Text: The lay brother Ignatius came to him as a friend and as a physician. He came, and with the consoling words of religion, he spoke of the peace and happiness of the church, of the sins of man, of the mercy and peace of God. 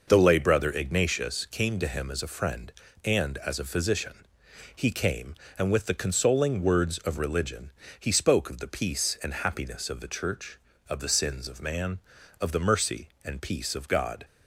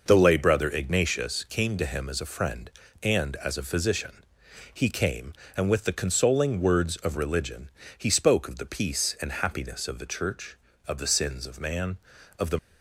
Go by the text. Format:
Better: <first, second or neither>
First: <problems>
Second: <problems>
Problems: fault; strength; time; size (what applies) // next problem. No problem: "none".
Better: first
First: none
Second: stops before "mercy and peace of God"; at 12.5 s